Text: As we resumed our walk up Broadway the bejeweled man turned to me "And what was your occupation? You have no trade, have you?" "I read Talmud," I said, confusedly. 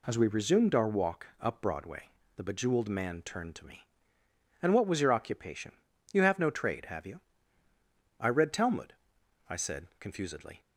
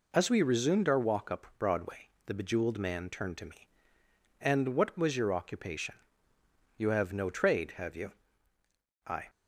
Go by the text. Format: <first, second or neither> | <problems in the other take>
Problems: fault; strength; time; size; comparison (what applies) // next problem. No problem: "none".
first | pauses between "Broadway" and "the"; slight; at 2.0 s; 0.16 s long; slight in the first // stops before "read Talmud I said confusedly"; at 9.2 s